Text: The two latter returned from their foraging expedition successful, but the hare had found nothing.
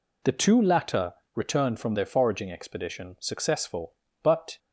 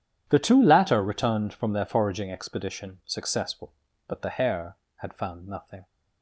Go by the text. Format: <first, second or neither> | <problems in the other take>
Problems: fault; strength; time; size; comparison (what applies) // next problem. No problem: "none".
second | pauses between "latter" and "returned"; slight; at 1.1 s; 0.19 s long // stops before "the hare had found nothing"; at 4.5 s